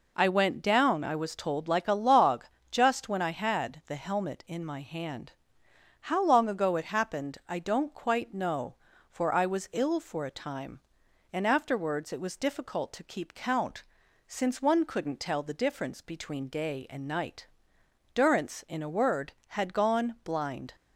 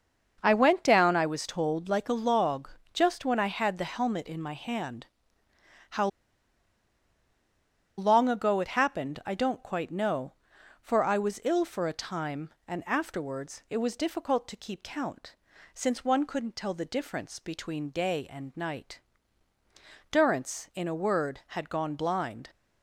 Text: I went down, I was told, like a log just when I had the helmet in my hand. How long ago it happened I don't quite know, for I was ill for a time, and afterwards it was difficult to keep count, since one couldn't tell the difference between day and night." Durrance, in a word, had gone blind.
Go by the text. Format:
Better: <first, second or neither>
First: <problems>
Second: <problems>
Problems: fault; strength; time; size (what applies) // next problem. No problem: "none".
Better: first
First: pauses between "log" and "just"; slight; at 2.4 s; 0.26 s long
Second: starts louder than the rest; until 1.4 s; 6 dB // pauses between "log" and "just"; slight; at 2.6 s; 0.24 s long // pauses between "How" and "long"; strong; at 6.0 s; 1.9 s long